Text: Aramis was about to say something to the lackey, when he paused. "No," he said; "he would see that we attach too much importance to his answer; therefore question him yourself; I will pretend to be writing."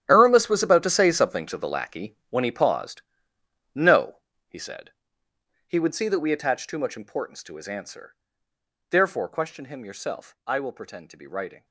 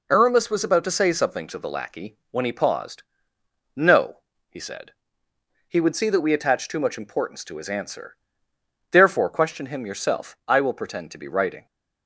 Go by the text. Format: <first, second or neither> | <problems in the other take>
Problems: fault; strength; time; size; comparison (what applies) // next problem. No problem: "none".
second | gets quieter; strong; throughout; 15 dB